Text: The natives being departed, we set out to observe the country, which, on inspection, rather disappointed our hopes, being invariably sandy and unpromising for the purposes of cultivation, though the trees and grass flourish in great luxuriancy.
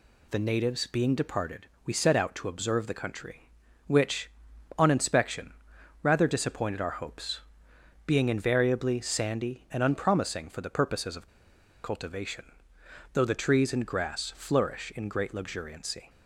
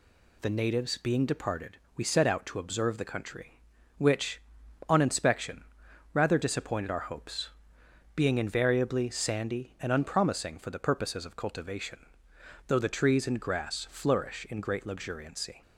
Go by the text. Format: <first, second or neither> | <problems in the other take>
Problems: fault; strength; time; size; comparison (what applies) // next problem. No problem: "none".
second | pauses between "of" and "cultivation"; noticeable; at 11.2 s; 0.57 s long